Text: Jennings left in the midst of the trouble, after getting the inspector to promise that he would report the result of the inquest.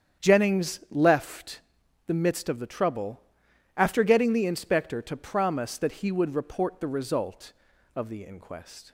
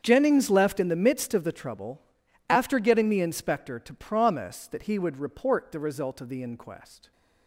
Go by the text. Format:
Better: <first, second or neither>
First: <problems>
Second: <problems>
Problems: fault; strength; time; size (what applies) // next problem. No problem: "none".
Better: second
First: starts louder than the rest; strong; until 1.3 s; 8.5 dB // skips "in"; at 1.8 s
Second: starts louder than the rest; strong; until 1.0 s; 7.5 dB